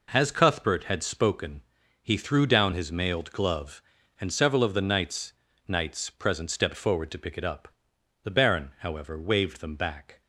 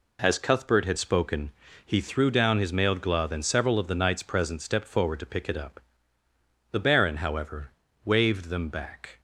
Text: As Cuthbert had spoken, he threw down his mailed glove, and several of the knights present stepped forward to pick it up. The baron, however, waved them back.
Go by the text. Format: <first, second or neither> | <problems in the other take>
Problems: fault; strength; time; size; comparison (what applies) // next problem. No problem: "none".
second | says "knights" twice; at 5.6 s